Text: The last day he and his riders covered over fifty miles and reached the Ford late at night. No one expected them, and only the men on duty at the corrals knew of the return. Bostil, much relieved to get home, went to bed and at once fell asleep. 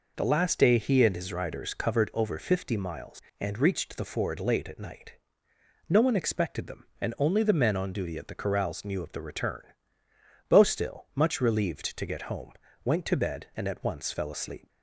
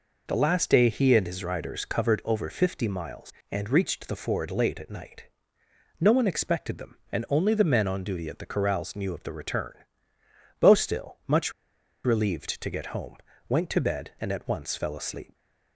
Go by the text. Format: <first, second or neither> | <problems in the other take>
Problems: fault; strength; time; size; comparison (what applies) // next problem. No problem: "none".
first | pauses between "much" and "relieved"; noticeable; at 11.5 s; 0.52 s long